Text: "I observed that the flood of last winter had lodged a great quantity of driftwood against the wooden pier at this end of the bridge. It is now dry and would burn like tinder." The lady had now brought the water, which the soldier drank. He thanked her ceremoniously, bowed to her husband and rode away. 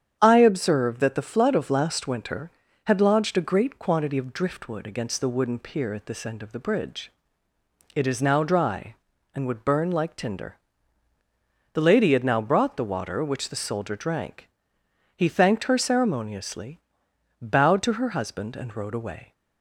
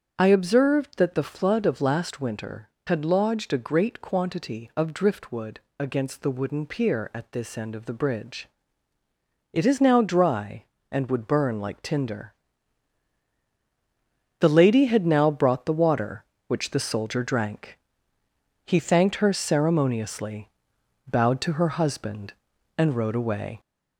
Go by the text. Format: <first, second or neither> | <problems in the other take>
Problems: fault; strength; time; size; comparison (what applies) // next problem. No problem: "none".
first | gets louder; slight; throughout; 3 dB // starts louder than the rest; strong; until 1.1 s; 7.5 dB; strong in the first // pauses between "driftwood" and "against"; slight; at 5.5 s; 0.20 s long